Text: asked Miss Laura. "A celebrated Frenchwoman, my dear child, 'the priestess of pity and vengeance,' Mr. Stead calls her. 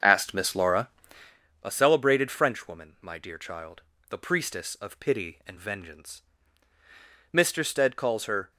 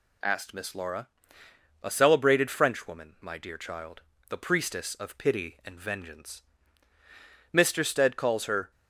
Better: second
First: starts louder than the rest; until 1.3 s; 6 dB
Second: none

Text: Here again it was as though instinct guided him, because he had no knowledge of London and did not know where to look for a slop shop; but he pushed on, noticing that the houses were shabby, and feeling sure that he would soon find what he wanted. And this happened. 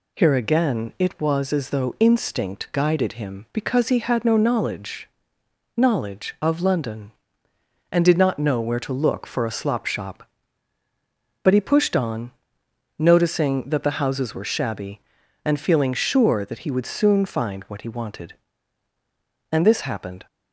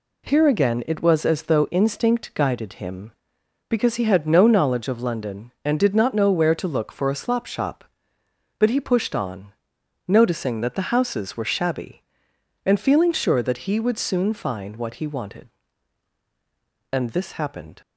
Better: second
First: says "knowledge" twice; at 5.7 s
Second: none

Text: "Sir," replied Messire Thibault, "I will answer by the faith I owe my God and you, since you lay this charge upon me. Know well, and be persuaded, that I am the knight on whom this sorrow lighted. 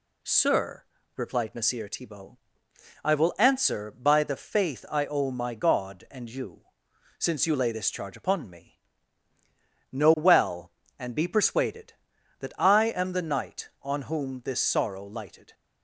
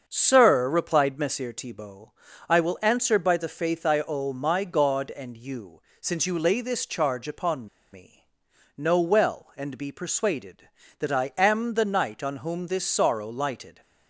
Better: first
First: none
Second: starts louder than the rest; until 1.0 s; 6.5 dB // pauses between "upon" and "me"; slight; at 7.6 s; 0.26 s long

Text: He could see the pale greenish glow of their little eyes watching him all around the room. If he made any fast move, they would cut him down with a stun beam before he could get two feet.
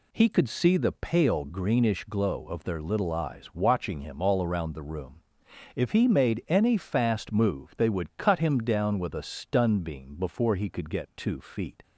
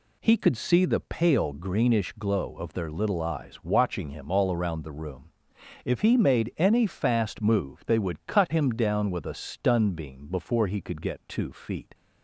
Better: neither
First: none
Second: none

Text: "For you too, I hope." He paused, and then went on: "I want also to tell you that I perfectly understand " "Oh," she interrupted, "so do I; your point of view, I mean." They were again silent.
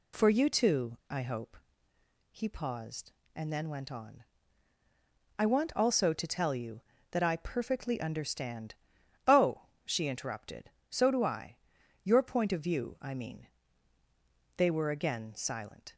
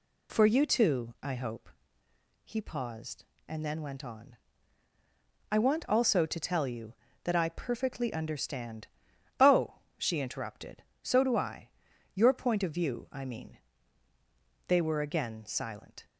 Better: neither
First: none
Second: none

